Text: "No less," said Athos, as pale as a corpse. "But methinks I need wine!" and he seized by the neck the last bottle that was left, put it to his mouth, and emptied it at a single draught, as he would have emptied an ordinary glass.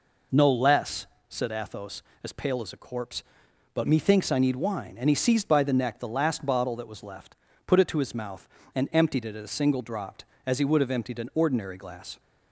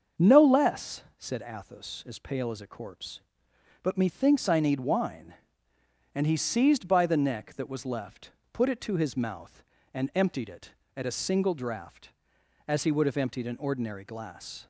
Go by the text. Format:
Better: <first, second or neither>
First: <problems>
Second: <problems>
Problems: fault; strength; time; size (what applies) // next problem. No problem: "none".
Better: first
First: none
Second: starts louder than the rest; until 1.3 s; 6.5 dB // skips "the last bottle"; at 7.5 s